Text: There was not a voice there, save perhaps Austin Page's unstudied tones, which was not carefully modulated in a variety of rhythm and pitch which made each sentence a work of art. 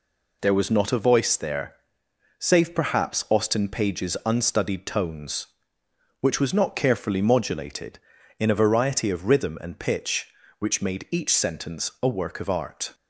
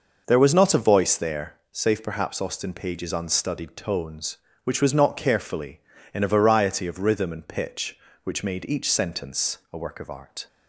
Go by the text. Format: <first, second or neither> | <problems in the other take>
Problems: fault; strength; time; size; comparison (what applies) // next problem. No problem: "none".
first | skips "modulated"; at 5.9 s